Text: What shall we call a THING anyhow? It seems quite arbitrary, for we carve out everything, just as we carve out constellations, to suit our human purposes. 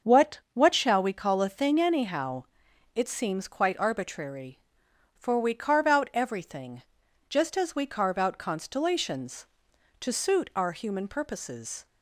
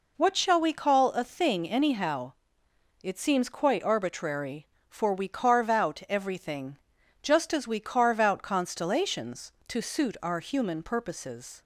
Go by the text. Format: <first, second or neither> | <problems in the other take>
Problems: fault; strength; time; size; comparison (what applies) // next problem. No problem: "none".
second | starts louder than the rest; until 1.1 s; 6.5 dB // says "What" twice; at 0.5 s